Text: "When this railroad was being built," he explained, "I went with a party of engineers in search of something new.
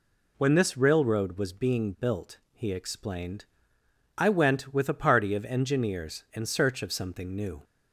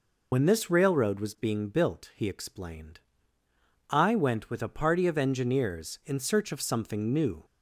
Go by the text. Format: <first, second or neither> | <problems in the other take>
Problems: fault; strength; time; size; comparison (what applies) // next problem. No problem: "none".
first | loses the start of "When"; at 0.3 s; 95 ms